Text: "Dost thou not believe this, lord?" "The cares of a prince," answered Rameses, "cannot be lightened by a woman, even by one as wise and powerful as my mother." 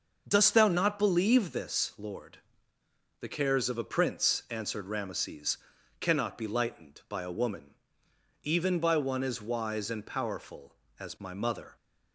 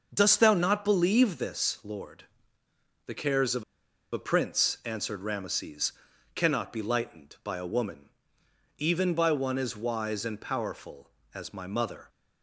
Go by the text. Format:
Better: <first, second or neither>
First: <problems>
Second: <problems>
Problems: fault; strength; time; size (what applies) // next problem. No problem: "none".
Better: first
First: starts louder than the rest; noticeable; until 1.2 s; 6 dB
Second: starts louder than the rest; noticeable; until 1.1 s; 6 dB // pauses between "of" and "a"; noticeable; at 3.6 s; 0.49 s long